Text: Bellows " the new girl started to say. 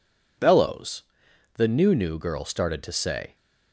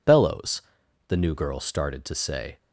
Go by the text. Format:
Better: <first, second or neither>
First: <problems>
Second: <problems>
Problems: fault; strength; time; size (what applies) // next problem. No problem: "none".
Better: second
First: says "new" twice; at 1.9 s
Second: none